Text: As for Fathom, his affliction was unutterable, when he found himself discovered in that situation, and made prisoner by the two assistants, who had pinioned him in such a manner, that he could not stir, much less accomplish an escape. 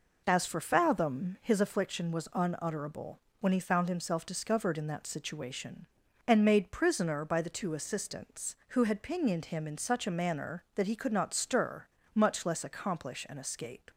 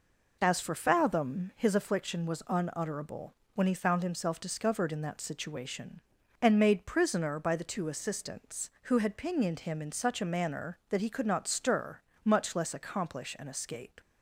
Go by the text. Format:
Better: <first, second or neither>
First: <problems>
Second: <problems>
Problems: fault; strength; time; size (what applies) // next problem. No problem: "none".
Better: neither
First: none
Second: none